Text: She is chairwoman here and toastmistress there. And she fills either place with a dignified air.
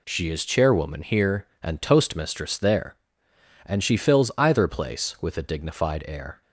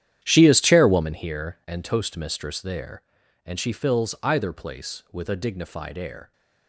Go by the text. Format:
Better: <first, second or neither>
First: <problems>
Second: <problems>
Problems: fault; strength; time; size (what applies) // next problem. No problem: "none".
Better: first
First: none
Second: starts louder than the rest; strong; until 1.2 s; 10.5 dB